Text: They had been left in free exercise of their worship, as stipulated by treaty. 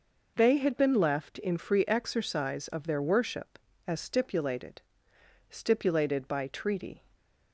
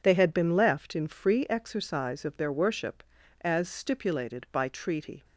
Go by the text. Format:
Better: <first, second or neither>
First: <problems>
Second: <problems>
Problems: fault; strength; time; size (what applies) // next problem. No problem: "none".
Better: second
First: says "stipulated" twice; at 5.4 s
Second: none